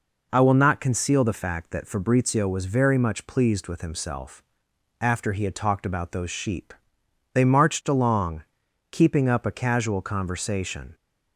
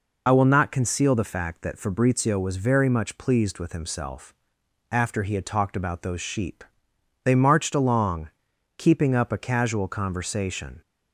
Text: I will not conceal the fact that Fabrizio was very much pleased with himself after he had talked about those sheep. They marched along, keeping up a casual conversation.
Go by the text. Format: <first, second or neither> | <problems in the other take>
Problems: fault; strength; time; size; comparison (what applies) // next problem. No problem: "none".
first | loses the start of "I"; at 0.2 s; 40 ms // pauses between "himself" and "after"; noticeable; at 4.3 s; 0.57 s long; noticeable in the first